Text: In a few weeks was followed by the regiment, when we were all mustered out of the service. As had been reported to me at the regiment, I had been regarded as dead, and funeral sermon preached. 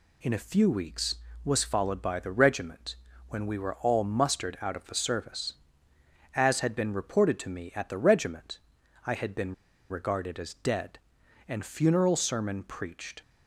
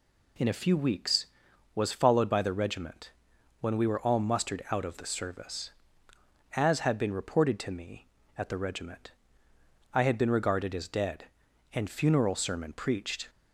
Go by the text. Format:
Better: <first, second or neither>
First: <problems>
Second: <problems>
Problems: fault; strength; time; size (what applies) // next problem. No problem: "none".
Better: second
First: pauses between "been" and "regarded"; at 9.5 s; 0.36 s long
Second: none